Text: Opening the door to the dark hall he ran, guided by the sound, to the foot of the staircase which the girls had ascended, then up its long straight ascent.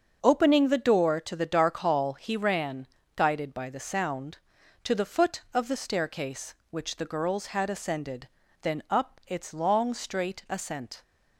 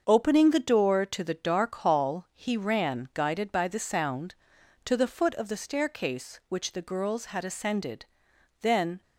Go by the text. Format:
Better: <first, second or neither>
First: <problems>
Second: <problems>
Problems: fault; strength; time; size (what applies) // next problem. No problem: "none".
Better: first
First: starts louder than the rest; until 1.2 s; 7 dB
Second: starts louder than the rest; until 1.0 s; 6.5 dB // stops before "up its long straight ascent"; at 9.0 s